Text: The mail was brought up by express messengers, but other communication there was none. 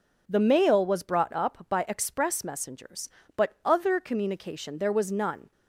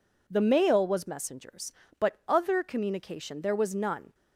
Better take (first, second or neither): first